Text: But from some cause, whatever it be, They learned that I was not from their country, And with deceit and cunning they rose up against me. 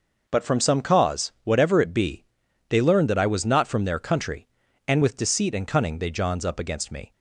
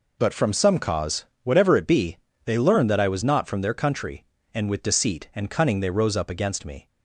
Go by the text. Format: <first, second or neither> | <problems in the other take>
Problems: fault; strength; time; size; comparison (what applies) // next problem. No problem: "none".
second | says "johns" for "rose"; at 6.1 s